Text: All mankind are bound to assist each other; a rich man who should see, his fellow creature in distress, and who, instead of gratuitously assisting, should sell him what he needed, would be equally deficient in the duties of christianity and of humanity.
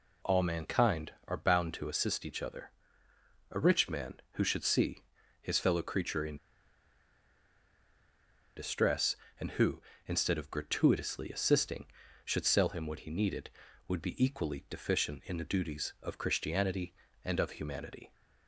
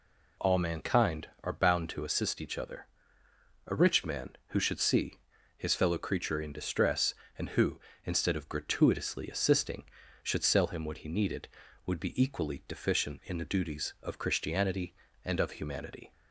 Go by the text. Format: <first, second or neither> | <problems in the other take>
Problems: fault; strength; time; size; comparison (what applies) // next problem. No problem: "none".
second | pauses between "in" and "distress"; strong; at 6.3 s; 2.2 s long